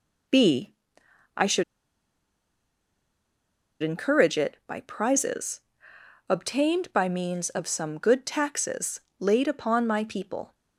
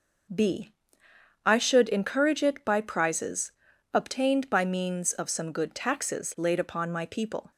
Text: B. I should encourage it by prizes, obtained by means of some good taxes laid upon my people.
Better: second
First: pauses between "should" and "encourage"; strong; at 1.6 s; 2.1 s long // pauses between "taxes" and "laid"; slight; at 9.0 s; 0.18 s long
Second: none

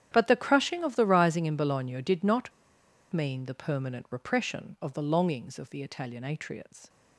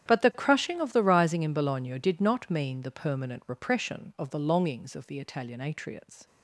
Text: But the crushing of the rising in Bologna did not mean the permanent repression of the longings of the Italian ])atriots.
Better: second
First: starts louder than the rest; strong; until 1.1 s; 10 dB // pauses between "not" and "mean"; noticeable; at 2.5 s; 0.61 s long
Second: starts louder than the rest; strong; until 1.1 s; 10 dB

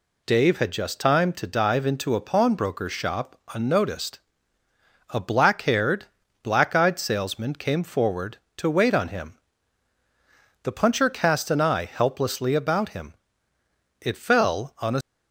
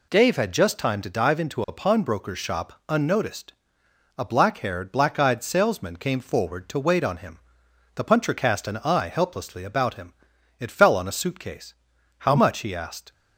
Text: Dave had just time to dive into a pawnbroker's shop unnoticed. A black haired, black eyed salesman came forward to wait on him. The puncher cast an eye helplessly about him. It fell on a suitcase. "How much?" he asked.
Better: second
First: stops before "suitcase How much he asked"; at 15.0 s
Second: none

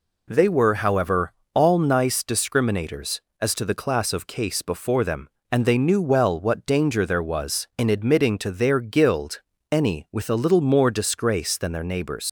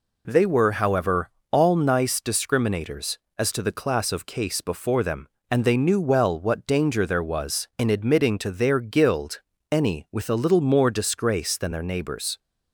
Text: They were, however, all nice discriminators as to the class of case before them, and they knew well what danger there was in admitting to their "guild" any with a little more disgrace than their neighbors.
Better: second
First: pauses between "guild" and "any"; slight; at 9.3 s; 0.32 s long // leaves "neighbors" unfinished; at 12.2 s; 95 ms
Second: pauses between "guild" and "any"; slight; at 9.3 s; 0.32 s long

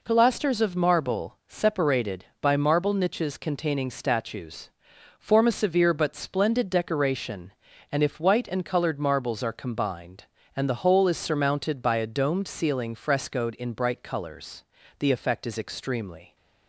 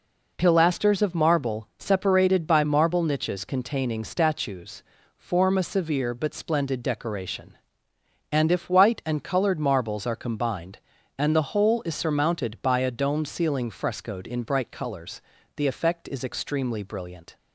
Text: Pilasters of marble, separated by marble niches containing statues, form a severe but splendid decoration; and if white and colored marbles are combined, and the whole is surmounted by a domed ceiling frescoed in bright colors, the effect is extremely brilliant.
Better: second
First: stops before "brilliant"; at 16.3 s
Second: none

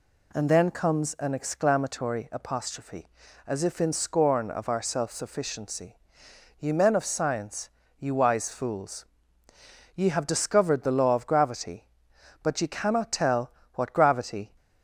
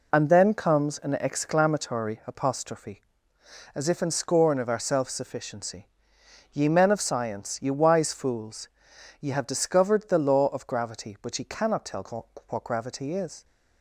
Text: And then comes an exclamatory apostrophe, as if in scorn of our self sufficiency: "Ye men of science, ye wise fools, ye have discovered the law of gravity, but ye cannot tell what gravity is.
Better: second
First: pauses between "tell" and "what"; slight; at 13.5 s; 0.22 s long // stops before "is"; at 14.5 s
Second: pauses between "tell" and "what"; slight; at 12.2 s; 0.22 s long

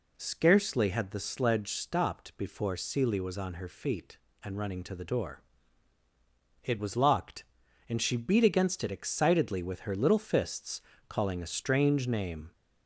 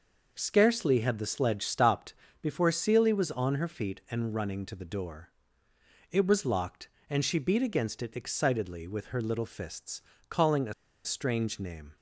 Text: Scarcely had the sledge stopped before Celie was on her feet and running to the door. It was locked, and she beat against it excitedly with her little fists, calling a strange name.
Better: first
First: none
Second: pauses between "stopped" and "before"; slight; at 2.1 s; 0.28 s long // pauses between "a" and "strange"; slight; at 10.7 s; 0.31 s long

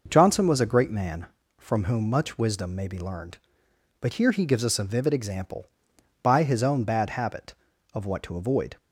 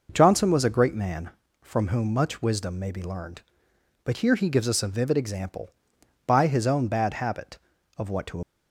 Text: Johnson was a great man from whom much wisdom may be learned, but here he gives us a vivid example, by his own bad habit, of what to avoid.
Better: first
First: none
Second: stops before "avoid"; at 8.4 s

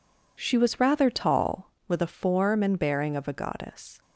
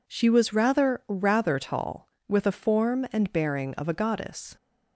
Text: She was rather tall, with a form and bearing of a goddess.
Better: first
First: none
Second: says "rather" twice; at 1.0 s

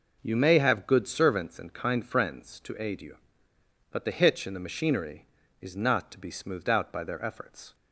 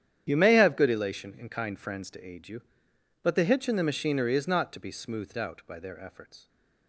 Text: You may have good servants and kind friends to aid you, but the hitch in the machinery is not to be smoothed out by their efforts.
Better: first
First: none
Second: starts louder than the rest; strong; until 1.2 s; 10 dB // says "elation" for "servants"; at 0.9 s

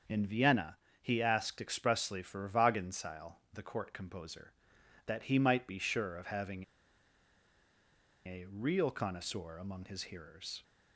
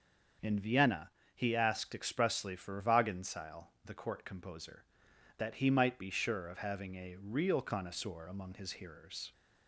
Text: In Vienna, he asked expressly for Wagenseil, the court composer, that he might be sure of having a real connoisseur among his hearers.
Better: second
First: starts louder than the rest; until 1.3 s; 6.5 dB // pauses between "having" and "a"; strong; at 6.6 s; 1.6 s long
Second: starts louder than the rest; until 1.6 s; 6 dB

